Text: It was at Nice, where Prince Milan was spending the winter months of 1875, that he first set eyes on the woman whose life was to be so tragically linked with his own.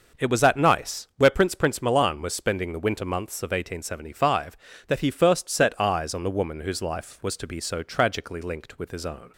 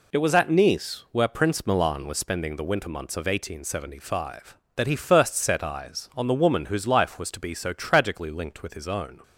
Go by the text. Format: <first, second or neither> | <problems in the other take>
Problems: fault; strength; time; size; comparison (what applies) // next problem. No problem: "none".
second | says "Prince" twice; at 1.5 s